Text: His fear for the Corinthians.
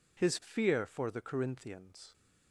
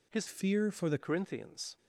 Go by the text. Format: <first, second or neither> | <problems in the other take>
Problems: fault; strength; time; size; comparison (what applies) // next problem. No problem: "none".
first | changes voice from "fear" to "the"; from 0.2 to 0.9 s; 0.7 s long